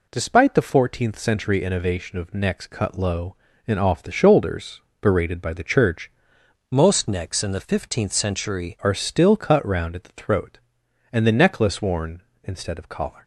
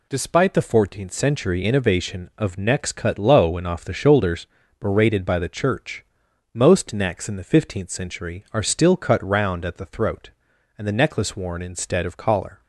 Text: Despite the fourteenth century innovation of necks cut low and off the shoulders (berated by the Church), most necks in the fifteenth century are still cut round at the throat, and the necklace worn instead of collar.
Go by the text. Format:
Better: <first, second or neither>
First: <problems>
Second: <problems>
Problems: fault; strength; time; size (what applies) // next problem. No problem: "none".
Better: second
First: changes voice from "most" to "century"; from 6.7 to 8.7 s; 2.0 s long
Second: none